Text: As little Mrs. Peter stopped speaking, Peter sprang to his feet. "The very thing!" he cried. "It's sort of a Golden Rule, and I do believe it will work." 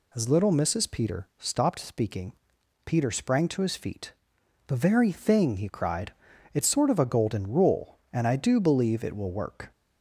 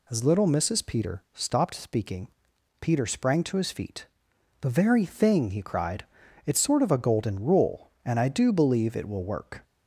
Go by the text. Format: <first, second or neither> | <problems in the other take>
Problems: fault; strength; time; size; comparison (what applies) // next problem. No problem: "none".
neither | none